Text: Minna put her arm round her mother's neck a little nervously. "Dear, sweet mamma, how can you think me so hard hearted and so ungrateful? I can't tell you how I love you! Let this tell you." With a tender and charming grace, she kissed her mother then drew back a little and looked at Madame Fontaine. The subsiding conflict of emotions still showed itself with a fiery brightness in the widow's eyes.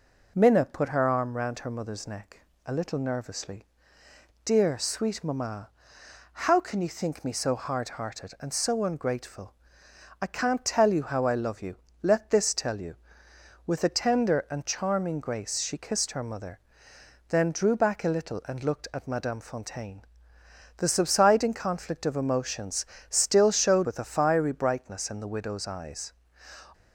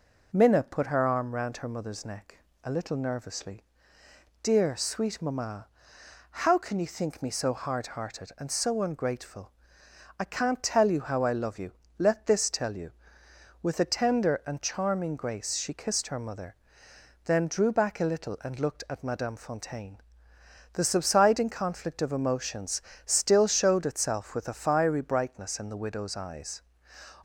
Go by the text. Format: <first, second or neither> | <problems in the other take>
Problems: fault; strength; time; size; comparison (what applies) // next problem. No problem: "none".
second | pauses between "neck" and "a"; slight; at 2.3 s; 0.26 s long; slight in the second // pauses between "mother" and "then"; noticeable; at 16.5 s; 0.68 s long; noticeable in the second // pauses between "emotions" and "still"; slight; at 22.8 s; 0.22 s long; slight in the second // skips "itself"; at 23.8 s